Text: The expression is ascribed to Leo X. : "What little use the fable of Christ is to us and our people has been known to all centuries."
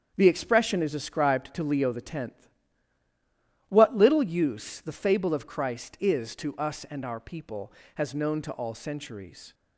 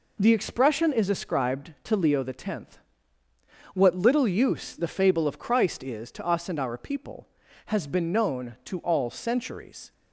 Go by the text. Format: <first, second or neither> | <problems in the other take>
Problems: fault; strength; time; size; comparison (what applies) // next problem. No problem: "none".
second | starts louder than the rest; strong; until 1.1 s; 7.5 dB // skips "been"; at 8.1 s